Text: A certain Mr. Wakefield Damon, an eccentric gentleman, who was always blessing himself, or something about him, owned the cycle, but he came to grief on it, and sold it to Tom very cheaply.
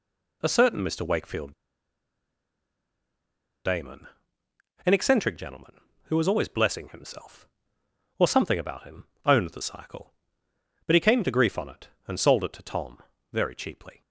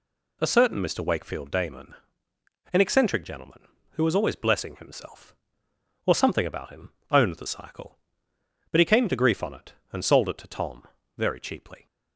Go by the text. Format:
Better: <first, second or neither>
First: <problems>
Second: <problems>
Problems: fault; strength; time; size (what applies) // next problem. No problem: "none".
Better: second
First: pauses between "Wakefield" and "Damon"; strong; at 1.5 s; 2.1 s long // pauses between "Tom" and "very"; slight; at 12.9 s; 0.34 s long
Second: pauses between "Tom" and "very"; slight; at 10.8 s; 0.34 s long